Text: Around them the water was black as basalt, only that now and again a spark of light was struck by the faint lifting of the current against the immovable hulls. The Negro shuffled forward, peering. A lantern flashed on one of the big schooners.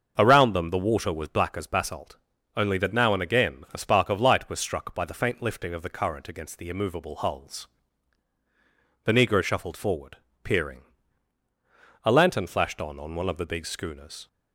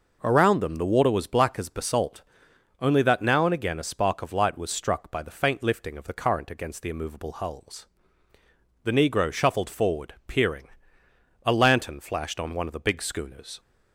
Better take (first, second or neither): second